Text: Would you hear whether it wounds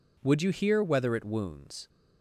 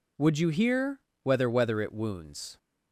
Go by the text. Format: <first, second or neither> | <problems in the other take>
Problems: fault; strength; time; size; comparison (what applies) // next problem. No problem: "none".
first | pauses between "hear" and "whether"; slight; at 1.0 s; 0.22 s long // says "whether" twice; at 1.4 s